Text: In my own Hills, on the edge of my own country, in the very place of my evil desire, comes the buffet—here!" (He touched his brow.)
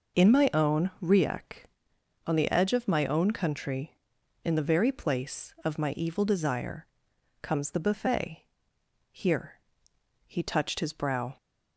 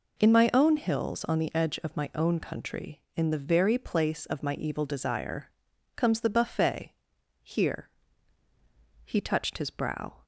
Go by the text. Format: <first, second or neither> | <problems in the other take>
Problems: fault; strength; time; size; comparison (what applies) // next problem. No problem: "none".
second | says "Riek" for "Hills"; at 1.0 s